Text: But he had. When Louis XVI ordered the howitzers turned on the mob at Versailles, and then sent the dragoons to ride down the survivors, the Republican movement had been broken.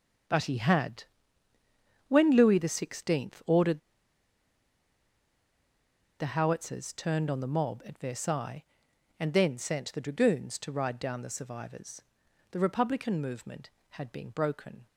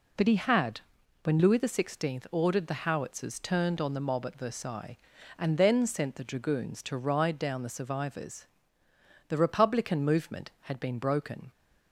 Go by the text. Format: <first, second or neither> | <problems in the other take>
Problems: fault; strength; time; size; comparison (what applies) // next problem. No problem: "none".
second | pauses between "ordered" and "the"; strong; at 3.7 s; 2.4 s long